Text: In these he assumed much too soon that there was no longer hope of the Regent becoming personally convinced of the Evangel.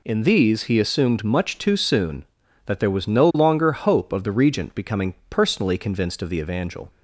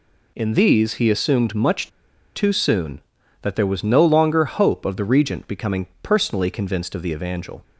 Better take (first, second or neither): first